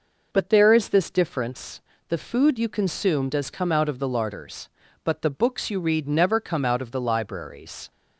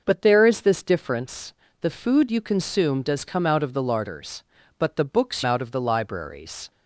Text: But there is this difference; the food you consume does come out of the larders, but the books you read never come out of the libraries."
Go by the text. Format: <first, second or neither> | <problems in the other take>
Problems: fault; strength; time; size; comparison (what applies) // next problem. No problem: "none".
first | skips "you read never come"; at 5.4 s